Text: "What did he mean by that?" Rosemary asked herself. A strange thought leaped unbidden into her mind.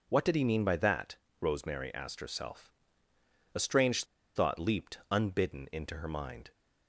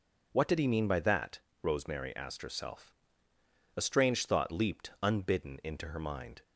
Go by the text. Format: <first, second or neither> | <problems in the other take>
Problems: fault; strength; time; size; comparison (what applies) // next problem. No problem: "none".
second | pauses between "strange" and "thought"; slight; at 4.0 s; 0.31 s long